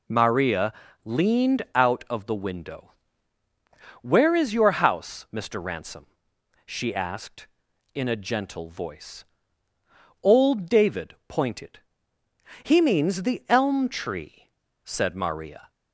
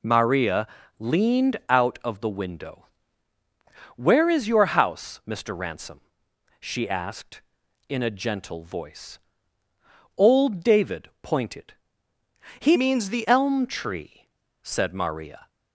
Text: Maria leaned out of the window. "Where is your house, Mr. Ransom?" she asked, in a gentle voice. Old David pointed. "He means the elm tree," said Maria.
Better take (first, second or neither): first